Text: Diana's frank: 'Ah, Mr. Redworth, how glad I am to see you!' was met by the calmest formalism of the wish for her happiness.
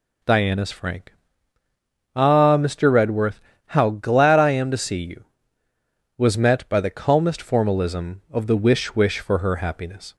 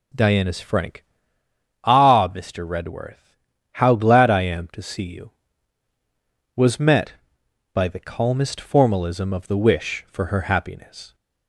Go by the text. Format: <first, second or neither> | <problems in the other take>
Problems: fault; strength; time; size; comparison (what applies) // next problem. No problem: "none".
second | says "wish" twice; at 8.9 s